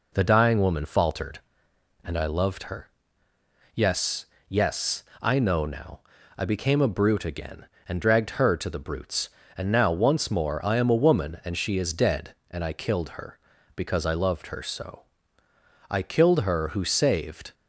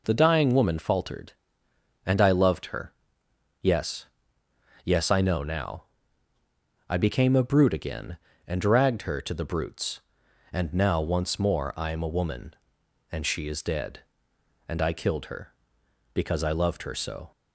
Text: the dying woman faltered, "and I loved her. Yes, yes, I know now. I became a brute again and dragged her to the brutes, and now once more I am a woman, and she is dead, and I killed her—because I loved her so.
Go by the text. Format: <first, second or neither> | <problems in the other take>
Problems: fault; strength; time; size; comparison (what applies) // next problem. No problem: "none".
second | goes on to say "I killed her who saved"; from 15.8 s on; 1.6 s long